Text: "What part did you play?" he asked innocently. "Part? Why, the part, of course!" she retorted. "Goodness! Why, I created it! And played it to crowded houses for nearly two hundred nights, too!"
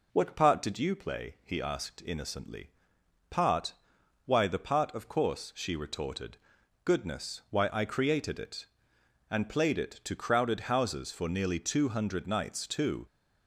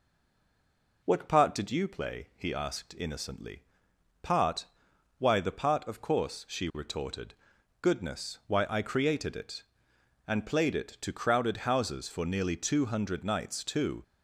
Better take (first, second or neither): first